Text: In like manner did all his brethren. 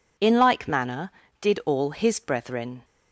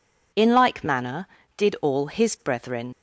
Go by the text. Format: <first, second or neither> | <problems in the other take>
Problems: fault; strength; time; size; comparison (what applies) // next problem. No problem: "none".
first | leaves "brethren" unfinished; at 2.9 s; 95 ms